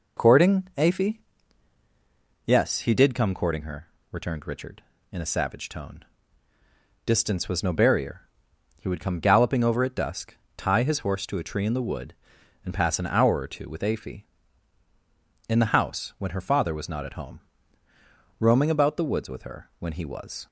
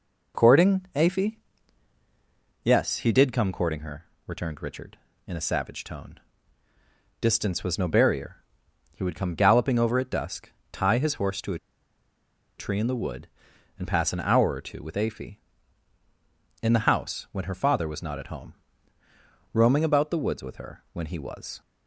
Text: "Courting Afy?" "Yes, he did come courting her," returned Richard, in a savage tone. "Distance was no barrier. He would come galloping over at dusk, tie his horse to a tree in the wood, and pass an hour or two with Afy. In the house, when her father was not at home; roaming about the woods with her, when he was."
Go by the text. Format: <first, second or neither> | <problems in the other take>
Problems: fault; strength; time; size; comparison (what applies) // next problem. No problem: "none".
first | pauses between "a" and "tree"; at 11.5 s; 1.0 s long